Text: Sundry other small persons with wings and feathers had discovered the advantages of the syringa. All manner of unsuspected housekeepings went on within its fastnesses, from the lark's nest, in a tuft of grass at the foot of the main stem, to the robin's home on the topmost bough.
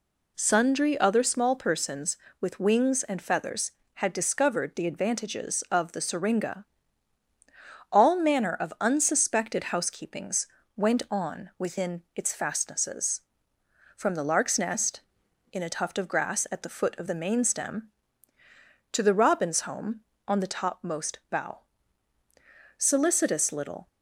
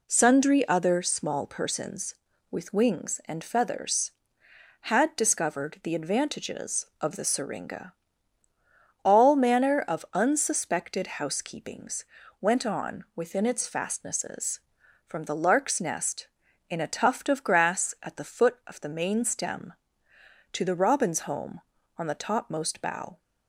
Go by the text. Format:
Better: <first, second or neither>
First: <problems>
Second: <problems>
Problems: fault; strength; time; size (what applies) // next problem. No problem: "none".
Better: second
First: pauses between "housekeepings" and "went"; slight; at 10.4 s; 0.28 s long // goes on to say "Solicitous little"; noticeable; from 22.7 s on; 1.1 s long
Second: pauses between "housekeepings" and "went"; at 12.0 s; 0.38 s long